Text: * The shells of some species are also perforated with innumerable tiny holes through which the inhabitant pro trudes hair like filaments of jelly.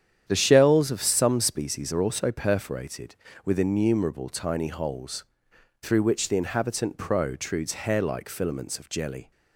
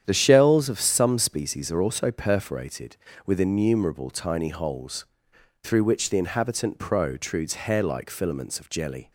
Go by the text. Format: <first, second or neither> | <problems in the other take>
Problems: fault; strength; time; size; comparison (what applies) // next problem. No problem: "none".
neither | starts louder than the rest; strong; the same in both // pauses between "holes" and "through"; noticeable; the same in both